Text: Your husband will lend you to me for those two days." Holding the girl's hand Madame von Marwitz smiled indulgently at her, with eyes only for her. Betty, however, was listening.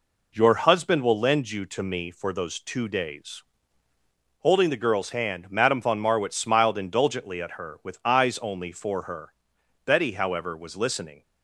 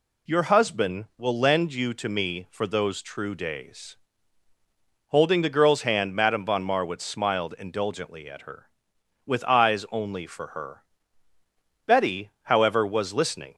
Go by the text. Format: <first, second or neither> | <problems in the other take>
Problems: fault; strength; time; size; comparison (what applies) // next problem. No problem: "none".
first | says "true" for "two"; at 3.0 s